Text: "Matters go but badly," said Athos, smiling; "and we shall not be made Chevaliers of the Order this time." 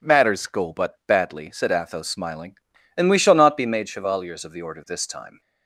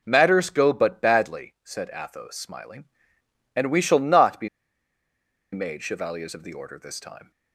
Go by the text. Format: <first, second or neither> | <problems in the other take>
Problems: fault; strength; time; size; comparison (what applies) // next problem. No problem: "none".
first | pauses between "be" and "made"; at 4.4 s; 1.0 s long